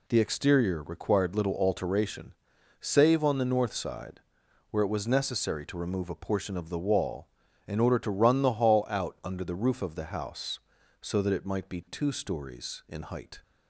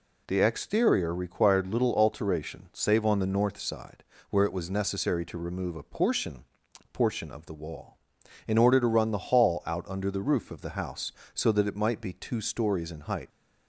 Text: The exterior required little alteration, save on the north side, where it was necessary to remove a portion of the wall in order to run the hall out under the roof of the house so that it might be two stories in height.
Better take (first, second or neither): first